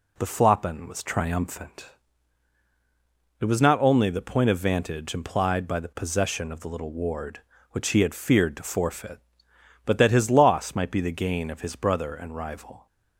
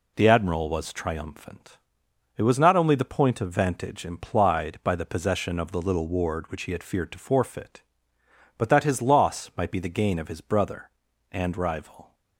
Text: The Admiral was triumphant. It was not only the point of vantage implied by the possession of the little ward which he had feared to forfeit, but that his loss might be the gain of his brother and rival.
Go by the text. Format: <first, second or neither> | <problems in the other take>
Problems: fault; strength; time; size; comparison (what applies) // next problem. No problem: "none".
second | says "Floppin" for "Admiral"; at 0.2 s